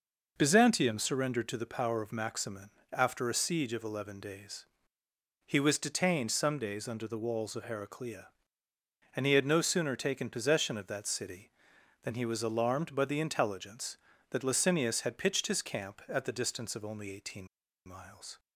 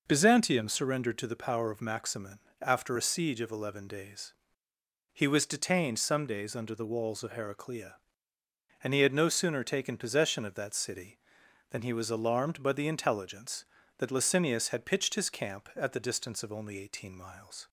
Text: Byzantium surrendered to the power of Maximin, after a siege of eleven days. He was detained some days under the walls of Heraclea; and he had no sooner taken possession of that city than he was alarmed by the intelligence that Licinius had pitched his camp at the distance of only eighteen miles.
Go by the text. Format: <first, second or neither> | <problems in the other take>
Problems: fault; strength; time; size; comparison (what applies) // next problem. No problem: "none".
second | pauses between "eighteen" and "miles"; at 17.4 s; 0.39 s long